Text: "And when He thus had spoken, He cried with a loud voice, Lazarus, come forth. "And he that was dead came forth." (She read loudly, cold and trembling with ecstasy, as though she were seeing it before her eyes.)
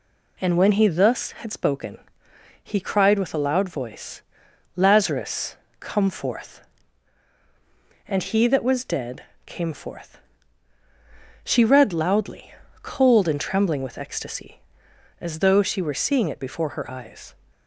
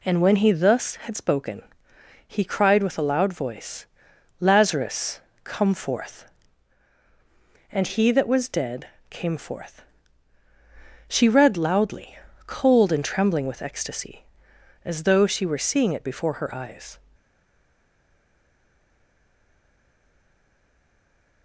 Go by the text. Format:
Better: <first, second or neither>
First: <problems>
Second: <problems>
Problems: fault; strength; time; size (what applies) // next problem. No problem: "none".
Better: first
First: pauses between "dead" and "came"; slight; at 9.2 s; 0.22 s long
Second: pauses between "dead" and "came"; slight; at 8.8 s; 0.22 s long // stays silent after the last word; strong; from 17.1 s on; 4.3 s long